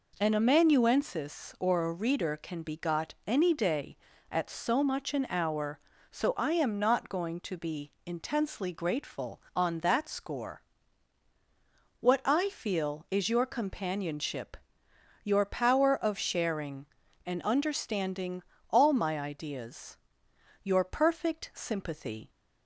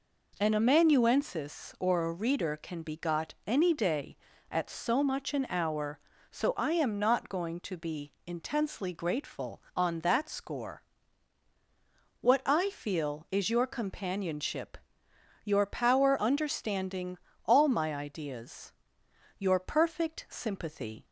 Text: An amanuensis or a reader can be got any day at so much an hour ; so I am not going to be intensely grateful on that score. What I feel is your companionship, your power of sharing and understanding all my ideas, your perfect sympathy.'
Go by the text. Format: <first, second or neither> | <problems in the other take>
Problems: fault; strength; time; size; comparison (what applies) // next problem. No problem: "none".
first | skips "of sharing and"; at 16.1 s // pauses between "understanding" and "all"; slight; at 17.1 s; 0.26 s long; slight in the first